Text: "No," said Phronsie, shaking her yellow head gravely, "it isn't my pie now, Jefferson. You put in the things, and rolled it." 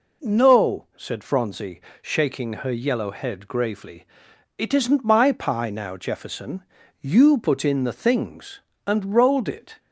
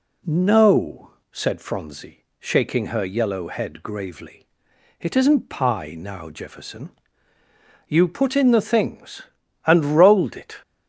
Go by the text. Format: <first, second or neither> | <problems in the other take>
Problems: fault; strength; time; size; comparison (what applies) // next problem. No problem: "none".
first | skips "my"; at 5.4 s